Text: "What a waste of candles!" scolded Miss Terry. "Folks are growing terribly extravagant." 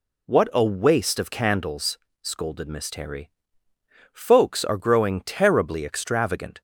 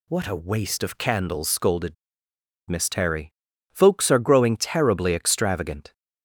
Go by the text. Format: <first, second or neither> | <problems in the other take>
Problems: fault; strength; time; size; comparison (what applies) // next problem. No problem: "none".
first | pauses between "scolded" and "Miss"; noticeable; at 1.9 s; 0.75 s long